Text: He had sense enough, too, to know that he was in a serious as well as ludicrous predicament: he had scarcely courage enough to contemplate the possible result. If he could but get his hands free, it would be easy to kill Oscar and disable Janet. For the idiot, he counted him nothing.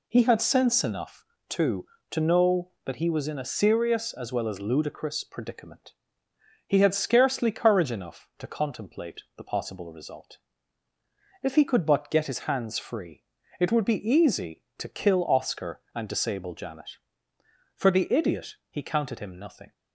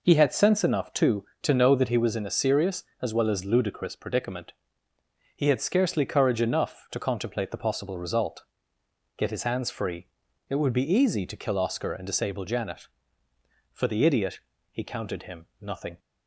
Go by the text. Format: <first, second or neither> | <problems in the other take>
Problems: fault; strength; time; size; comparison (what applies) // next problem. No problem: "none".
first | skips "If he could but"; at 8.8 s // pauses between "him" and "nothing"; slight; at 15.4 s; 0.16 s long